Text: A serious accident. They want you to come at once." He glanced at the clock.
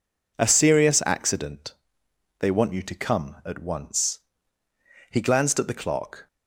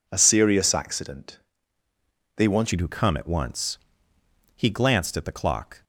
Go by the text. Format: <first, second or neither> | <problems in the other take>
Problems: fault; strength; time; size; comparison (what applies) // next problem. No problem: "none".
first | changes voice at "you"; from 2.7 s on; 3.1 s long